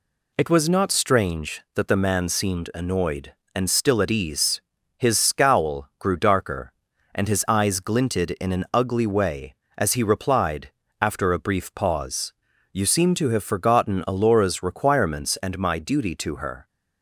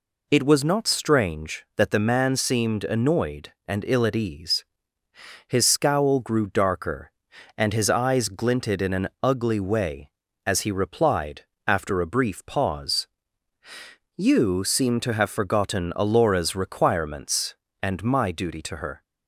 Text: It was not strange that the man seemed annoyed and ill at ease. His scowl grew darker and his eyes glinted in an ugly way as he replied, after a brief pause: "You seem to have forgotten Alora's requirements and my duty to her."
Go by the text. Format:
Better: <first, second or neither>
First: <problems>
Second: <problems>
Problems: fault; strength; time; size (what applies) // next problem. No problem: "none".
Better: second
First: says "still" for "ill"; at 3.6 s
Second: none